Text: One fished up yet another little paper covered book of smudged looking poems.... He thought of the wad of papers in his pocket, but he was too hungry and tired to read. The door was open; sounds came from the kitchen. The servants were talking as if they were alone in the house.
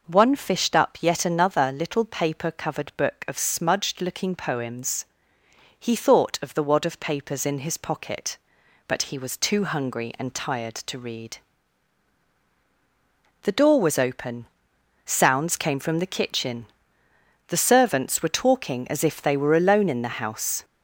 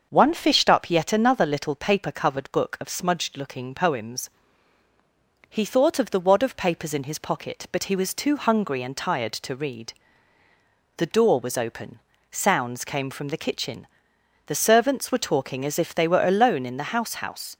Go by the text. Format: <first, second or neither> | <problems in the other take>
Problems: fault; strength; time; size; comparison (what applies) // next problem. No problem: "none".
first | starts louder than the rest; until 1.1 s; 6.5 dB // says "house" twice; at 17.1 s